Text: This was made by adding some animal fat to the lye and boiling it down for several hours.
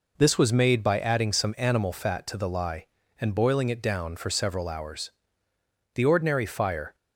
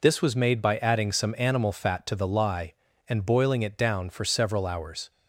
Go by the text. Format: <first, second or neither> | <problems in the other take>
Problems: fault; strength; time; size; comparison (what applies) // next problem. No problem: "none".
second | goes on to say "The ordinary fire"; noticeable; from 5.9 s on; 1.0 s long